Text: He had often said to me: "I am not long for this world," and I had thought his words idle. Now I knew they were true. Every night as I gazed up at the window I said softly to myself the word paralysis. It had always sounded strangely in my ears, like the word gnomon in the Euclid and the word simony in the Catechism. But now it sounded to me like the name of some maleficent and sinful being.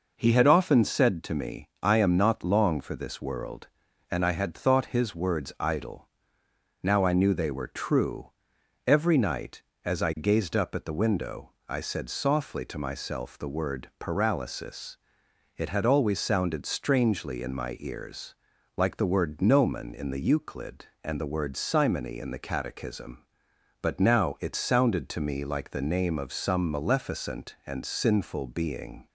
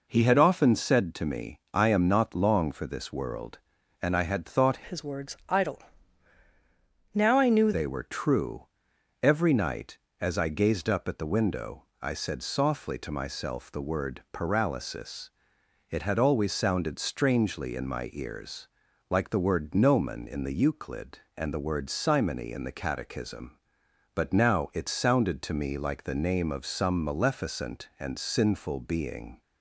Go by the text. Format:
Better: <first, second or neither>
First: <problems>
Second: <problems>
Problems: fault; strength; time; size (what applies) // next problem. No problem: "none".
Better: first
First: pauses between "window" and "I"; slight; at 11.5 s; 0.16 s long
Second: changes voice from "his" to "knew"; from 4.8 to 7.7 s; 2.9 s long // pauses between "window" and "I"; slight; at 11.8 s; 0.16 s long